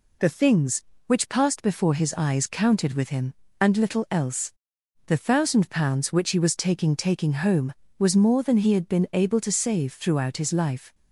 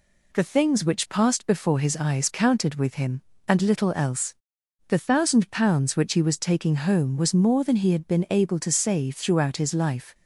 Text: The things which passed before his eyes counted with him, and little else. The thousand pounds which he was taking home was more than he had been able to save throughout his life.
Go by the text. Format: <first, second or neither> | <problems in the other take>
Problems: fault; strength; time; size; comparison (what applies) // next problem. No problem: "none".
second | says "taking" twice; at 6.9 s